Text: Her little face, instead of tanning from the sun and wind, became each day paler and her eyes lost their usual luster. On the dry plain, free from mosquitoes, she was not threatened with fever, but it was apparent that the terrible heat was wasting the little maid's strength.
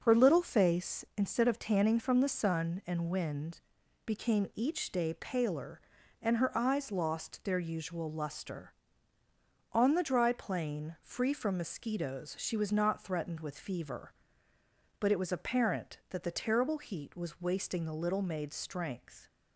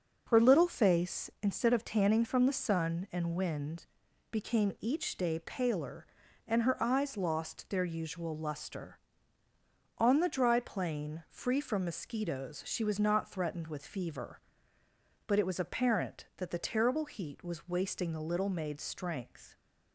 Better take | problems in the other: neither | none

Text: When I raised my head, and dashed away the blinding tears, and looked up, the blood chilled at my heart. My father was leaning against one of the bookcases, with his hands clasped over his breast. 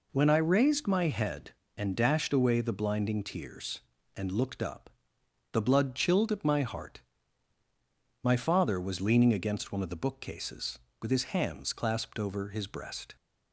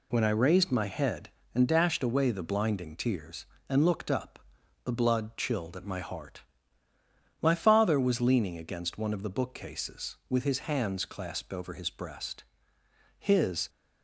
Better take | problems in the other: first | goes on to say "His"; from 13.1 s on; 0.50 s long

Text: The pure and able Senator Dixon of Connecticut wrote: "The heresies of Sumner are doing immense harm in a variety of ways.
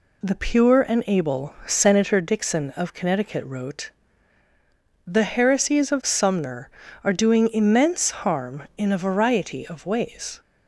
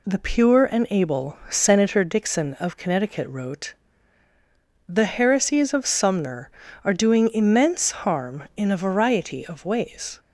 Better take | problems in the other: neither | none

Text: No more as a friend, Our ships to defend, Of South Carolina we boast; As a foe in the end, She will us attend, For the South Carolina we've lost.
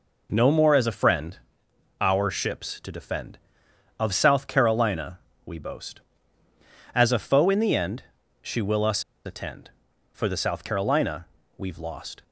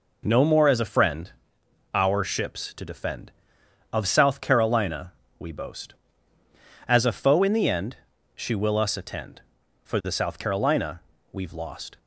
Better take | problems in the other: second | pauses between "Carolina" and "we"; slight; at 5.1 s; 0.26 s long; slight in the second // pauses between "us" and "attend"; slight; at 9.0 s; 0.22 s long // pauses between "Carolina" and "we've"; slight; at 11.2 s; 0.32 s long; slight in the second

